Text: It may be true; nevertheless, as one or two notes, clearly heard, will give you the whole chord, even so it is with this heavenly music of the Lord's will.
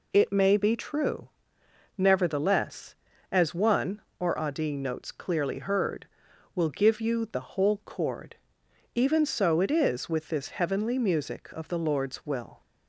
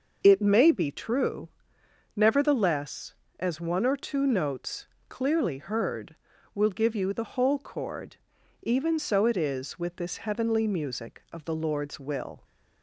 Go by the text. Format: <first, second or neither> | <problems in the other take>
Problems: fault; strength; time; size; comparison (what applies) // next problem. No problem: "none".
second | says "adi" for "two"; at 4.3 s